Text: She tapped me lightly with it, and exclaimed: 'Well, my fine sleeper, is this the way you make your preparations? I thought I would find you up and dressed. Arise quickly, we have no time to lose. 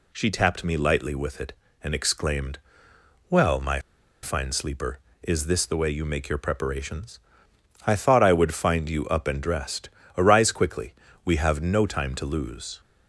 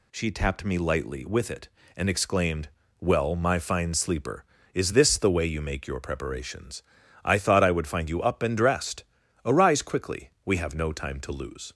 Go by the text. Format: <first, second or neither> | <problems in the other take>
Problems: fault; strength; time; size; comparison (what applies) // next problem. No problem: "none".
second | pauses between "my" and "fine"; at 3.7 s; 0.44 s long